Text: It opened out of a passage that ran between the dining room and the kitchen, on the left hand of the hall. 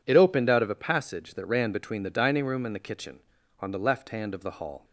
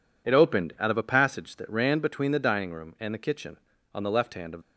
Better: first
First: none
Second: stops before "the hall"; at 4.6 s

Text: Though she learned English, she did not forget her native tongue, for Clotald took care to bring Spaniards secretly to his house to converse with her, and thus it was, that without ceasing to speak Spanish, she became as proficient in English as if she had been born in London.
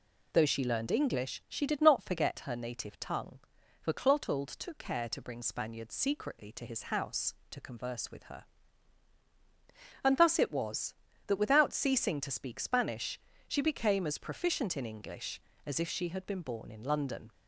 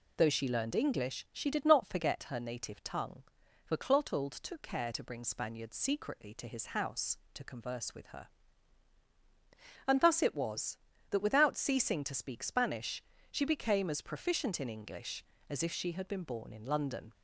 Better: neither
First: none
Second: none

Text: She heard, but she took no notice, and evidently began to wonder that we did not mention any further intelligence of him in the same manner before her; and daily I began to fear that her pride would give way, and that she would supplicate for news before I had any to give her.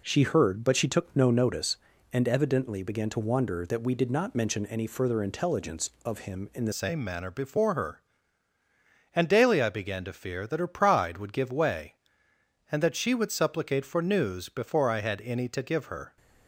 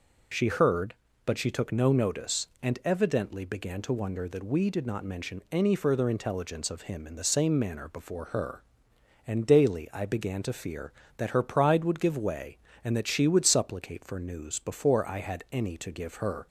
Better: second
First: changes voice at "same"; from 6.7 s on; 9.4 s long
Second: none

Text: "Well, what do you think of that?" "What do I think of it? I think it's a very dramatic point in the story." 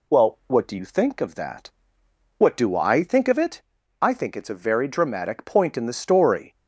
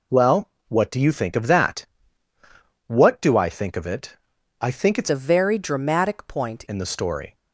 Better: first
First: none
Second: changes voice from "a" to "point"; from 5.0 to 6.6 s; 1.6 s long

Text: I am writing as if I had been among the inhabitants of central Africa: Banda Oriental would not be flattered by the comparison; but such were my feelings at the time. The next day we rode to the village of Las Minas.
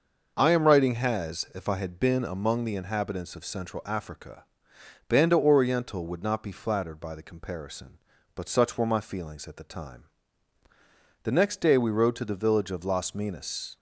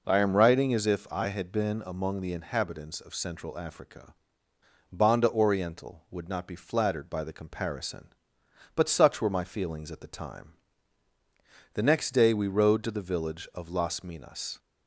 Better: second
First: starts louder than the rest; noticeable; until 1.3 s; 6 dB // says "has" for "as"; at 0.9 s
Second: none

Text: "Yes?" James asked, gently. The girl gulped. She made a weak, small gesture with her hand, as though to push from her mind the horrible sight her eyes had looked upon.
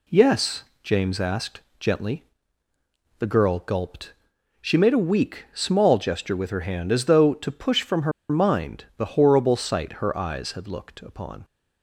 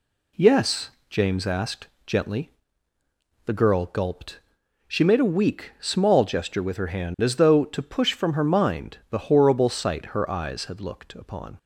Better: second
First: pauses between "her" and "mind"; slight; at 8.1 s; 0.19 s long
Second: none

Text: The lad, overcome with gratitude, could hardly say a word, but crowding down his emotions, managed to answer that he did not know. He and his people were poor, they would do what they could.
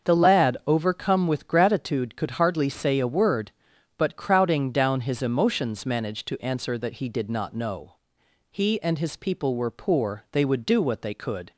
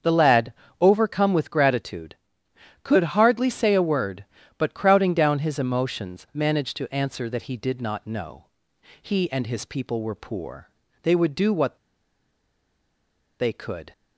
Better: first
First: starts louder than the rest; until 1.1 s; 6.5 dB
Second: starts louder than the rest; until 1.2 s; 7 dB // pauses between "what" and "they"; strong; at 11.7 s; 1.6 s long

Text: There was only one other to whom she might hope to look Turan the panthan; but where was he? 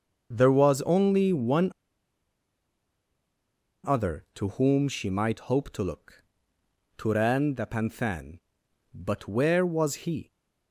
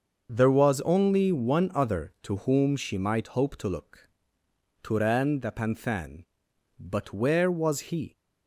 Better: second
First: starts louder than the rest; until 1.3 s; 6.5 dB // pauses between "one" and "other"; strong; at 1.7 s; 2.1 s long // pauses between "look" and "Turan"; noticeable; at 6.2 s; 0.74 s long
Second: starts louder than the rest; until 1.3 s; 6.5 dB // pauses between "look" and "Turan"; noticeable; at 4.0 s; 0.74 s long

